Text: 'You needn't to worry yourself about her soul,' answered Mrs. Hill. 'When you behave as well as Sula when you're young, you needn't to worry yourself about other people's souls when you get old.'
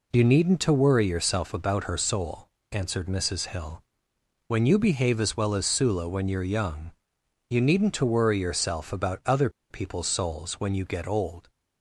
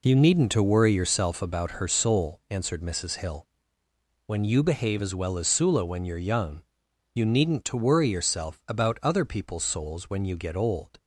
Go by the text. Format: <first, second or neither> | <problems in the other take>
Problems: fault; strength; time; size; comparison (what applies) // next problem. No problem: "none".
second | pauses between "other" and "people's"; slight; at 9.4 s; 0.21 s long